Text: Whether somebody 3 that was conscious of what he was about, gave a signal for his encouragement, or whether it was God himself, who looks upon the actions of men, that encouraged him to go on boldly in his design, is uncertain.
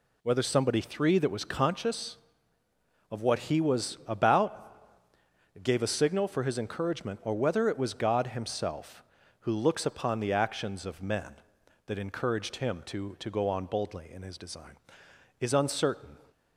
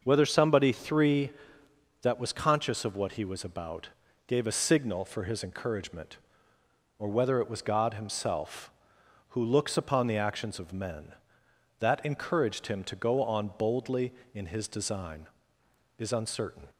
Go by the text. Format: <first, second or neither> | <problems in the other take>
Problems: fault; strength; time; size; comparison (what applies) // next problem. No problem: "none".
second | says "to" twice; at 13.1 s